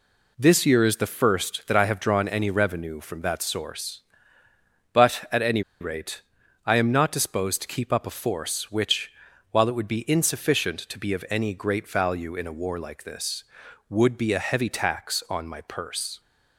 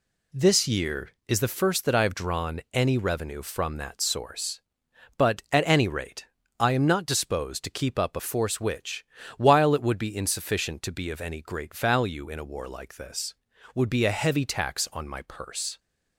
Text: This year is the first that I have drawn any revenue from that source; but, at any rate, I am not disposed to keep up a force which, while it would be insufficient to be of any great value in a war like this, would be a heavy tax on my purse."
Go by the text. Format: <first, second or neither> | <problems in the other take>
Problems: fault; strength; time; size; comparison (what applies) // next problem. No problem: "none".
second | pauses between "any" and "rate"; slight; at 5.6 s; 0.18 s long